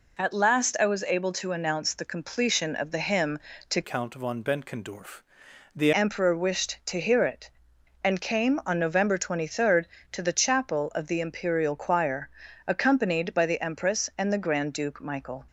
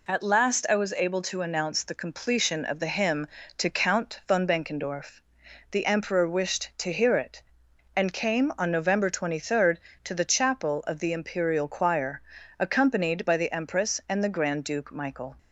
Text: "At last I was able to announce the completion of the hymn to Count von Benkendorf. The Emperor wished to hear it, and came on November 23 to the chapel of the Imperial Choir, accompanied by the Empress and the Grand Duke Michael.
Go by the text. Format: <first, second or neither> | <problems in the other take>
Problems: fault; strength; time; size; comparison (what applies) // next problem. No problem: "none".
second | changes voice from "Count" to "The"; from 3.8 to 5.9 s; 2.1 s long